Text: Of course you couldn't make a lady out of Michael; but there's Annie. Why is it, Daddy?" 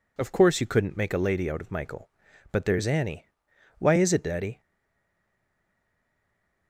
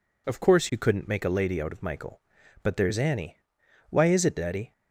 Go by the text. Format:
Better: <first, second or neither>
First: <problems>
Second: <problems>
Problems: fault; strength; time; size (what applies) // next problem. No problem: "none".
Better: second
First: stays silent after the last word; from 4.5 s on; 2.1 s long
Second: none